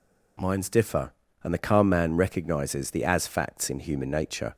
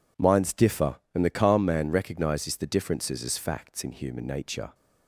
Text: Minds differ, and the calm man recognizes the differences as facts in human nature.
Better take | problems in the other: second | skips "differences"; at 3.0 s

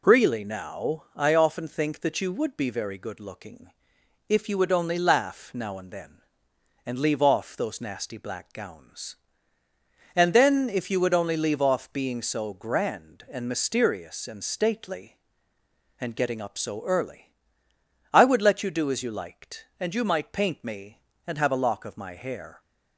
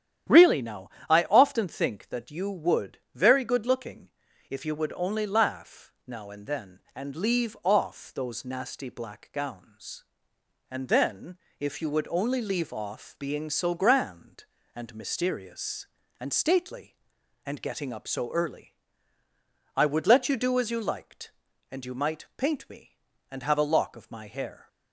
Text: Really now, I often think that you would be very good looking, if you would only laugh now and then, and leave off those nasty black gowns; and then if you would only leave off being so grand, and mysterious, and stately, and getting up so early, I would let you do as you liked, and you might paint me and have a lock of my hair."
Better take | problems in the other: first | starts louder than the rest; strong; until 1.5 s; 10 dB // skips "be"; at 3.0 s // pauses between "then" and "if"; slight; at 11.3 s; 0.22 s long

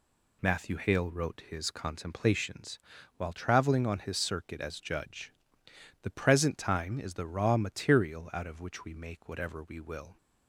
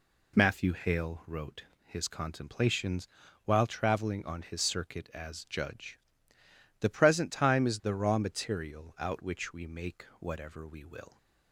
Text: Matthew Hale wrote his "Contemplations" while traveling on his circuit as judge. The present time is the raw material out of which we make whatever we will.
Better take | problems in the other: first | pauses between "wrote" and "his"; slight; at 1.6 s; 0.22 s long // pauses between "Contemplations" and "while"; at 3.0 s; 0.38 s long; also in the first // skips "of"; at 9.2 s

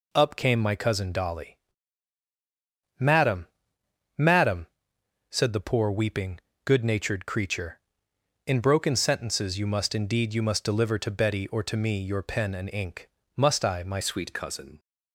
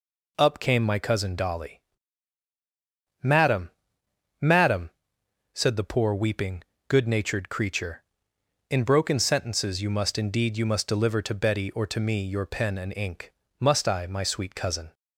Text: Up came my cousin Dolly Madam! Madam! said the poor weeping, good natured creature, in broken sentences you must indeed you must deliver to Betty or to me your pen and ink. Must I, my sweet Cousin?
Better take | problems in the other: second | pauses between "Dolly" and "Madam"; strong; at 1.5 s; 1.4 s long; strong in the second // changes voice at "sweet"; from 14.0 s on; 0.7 s long

